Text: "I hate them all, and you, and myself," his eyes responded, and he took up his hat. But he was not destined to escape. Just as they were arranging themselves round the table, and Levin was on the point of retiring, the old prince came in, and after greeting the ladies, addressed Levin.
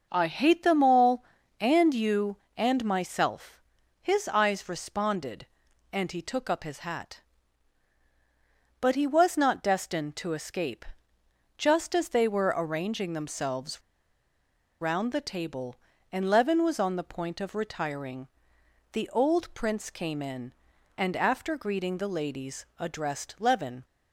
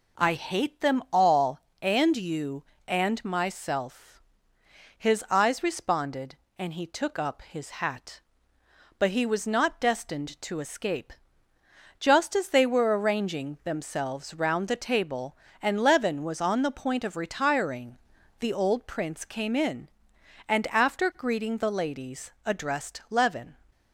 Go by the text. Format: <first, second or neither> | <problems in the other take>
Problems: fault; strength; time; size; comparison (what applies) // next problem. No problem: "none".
second | pauses between "themselves" and "round"; at 13.8 s; 1.0 s long